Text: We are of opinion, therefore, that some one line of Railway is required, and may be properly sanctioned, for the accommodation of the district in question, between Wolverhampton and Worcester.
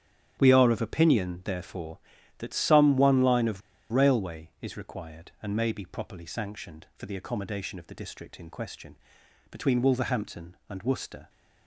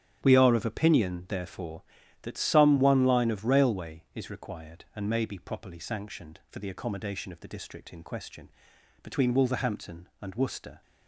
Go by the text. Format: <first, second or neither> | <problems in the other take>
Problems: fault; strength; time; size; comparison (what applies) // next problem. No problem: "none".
second | starts louder than the rest; strong; until 1.4 s; 10.5 dB; strong in the second // pauses between "of" and "Railway"; slight; at 3.6 s; 0.32 s long